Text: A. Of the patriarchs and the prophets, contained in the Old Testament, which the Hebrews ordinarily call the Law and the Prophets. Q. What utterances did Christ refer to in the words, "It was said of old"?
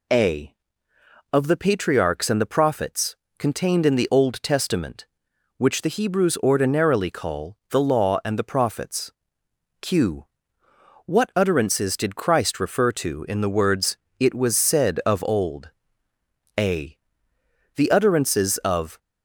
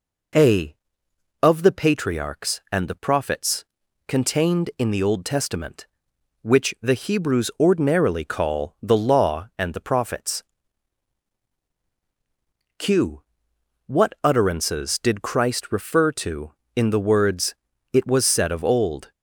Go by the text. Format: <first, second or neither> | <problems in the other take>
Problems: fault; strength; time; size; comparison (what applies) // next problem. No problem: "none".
second | goes on to say "A The utterances of"; strong; from 16.5 s on; 2.4 s long